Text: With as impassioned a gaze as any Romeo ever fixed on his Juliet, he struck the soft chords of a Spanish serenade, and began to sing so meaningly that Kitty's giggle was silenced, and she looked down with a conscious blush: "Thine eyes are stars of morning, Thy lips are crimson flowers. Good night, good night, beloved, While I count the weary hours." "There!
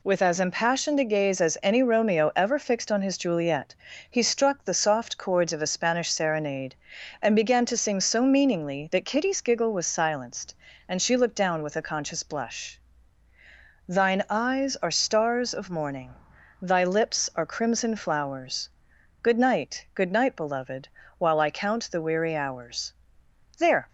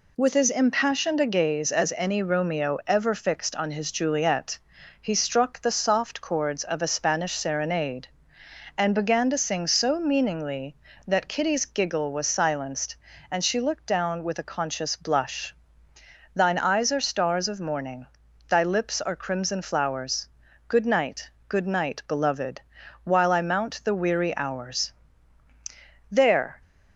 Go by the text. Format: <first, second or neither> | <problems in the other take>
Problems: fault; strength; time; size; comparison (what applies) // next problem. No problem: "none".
first | says "mount" for "count"; at 23.4 s